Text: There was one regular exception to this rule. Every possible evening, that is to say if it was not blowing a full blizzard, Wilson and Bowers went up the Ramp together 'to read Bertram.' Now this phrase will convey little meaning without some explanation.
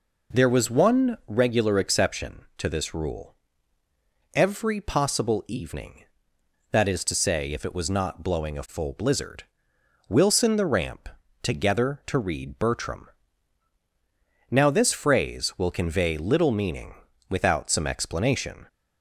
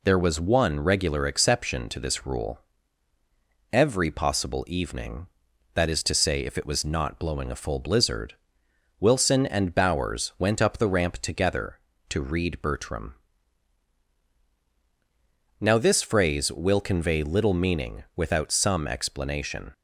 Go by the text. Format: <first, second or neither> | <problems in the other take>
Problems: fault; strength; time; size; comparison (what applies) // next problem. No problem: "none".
second | skips "and Bowers went up"; at 10.5 s // pauses between "Ramp" and "together"; slight; at 11.0 s; 0.36 s long // pauses between "meaning" and "without"; slight; at 16.9 s; 0.34 s long